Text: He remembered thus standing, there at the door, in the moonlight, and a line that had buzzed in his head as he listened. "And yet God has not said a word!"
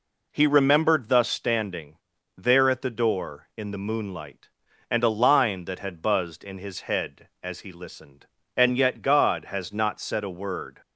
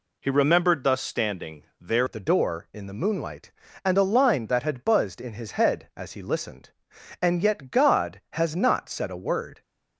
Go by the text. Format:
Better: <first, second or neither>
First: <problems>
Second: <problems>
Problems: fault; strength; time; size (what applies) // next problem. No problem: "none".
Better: first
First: none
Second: changes voice at "at"; from 2.0 s on; 7.6 s long